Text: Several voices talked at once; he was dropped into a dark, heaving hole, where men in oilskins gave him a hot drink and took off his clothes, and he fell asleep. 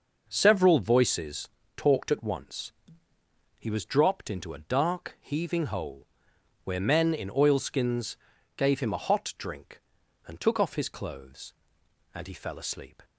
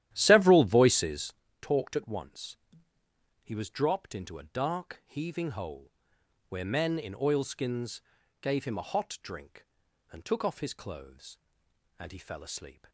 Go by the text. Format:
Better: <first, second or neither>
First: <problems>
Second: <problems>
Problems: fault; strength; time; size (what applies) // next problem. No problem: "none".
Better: first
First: pauses between "voices" and "talked"; slight; at 1.4 s; 0.28 s long // pauses between "oilskins" and "gave"; at 8.1 s; 0.40 s long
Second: starts louder than the rest; strong; until 1.5 s; 12.5 dB // pauses between "voices" and "talked"; slight; at 1.3 s; 0.28 s long // pauses between "oilskins" and "gave"; at 8.0 s; 0.40 s long